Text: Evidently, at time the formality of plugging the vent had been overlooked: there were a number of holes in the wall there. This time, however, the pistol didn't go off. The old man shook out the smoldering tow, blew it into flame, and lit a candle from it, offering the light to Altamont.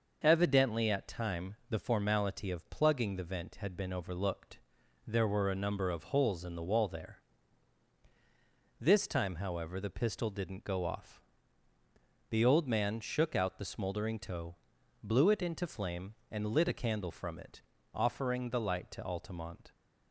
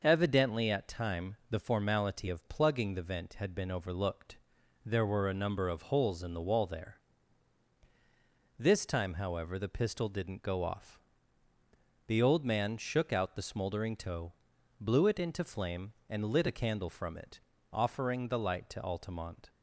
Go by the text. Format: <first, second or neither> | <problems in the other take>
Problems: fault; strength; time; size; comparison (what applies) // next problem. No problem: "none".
neither | none